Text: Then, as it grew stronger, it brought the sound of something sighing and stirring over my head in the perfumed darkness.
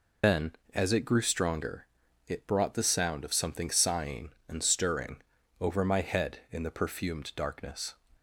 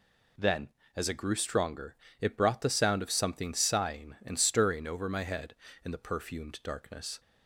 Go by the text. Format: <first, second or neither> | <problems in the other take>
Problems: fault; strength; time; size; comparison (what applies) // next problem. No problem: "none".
second | loses the start of "Then"; at 0.2 s; 155 ms // pauses between "stirring" and "over"; at 5.1 s; 0.40 s long